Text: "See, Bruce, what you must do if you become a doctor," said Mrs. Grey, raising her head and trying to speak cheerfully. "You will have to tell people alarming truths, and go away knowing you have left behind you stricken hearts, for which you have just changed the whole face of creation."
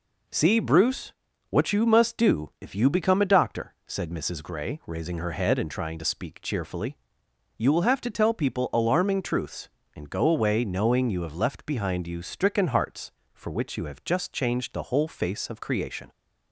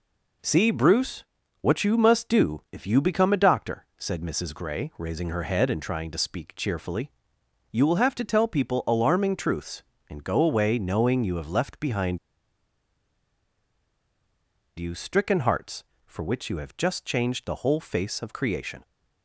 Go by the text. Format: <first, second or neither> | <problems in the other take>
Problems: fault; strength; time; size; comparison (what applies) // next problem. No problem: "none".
first | pauses between "behind" and "you"; strong; at 12.1 s; 2.6 s long